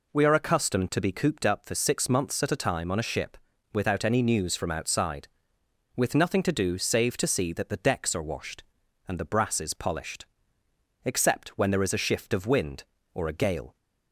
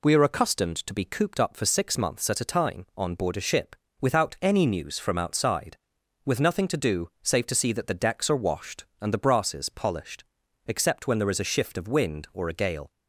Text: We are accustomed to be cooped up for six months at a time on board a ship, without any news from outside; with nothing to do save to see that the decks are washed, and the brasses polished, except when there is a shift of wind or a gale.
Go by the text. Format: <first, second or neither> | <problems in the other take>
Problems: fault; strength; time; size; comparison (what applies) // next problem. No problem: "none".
second | skips "board"; at 2.9 s